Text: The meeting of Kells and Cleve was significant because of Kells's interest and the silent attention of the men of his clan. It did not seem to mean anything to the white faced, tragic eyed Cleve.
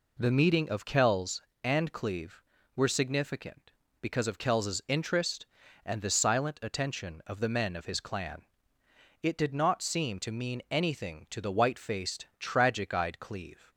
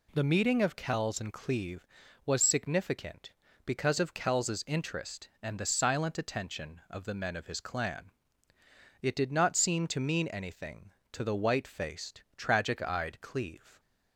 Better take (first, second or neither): second